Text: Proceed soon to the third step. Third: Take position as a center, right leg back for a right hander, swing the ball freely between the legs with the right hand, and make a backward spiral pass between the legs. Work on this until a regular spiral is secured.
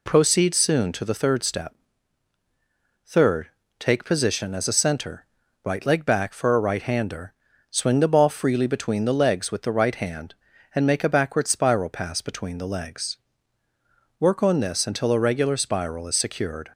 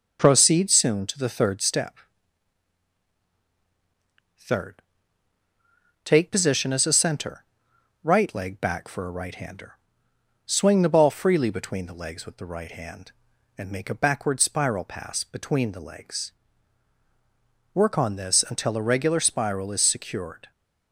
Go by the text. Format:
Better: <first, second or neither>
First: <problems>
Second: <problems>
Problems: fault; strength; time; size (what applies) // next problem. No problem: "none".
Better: neither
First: none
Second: none